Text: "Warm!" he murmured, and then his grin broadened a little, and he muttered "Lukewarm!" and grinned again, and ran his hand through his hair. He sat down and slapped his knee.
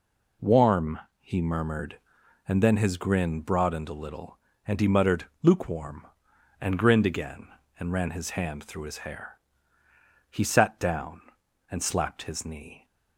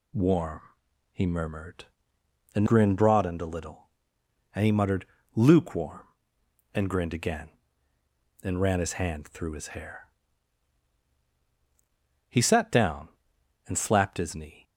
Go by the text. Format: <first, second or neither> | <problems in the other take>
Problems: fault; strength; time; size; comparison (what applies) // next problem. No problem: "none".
first | skips "then his"; at 2.6 s // pauses between "muttered" and "Lukewarm"; slight; at 5.0 s; 0.30 s long; slight in the first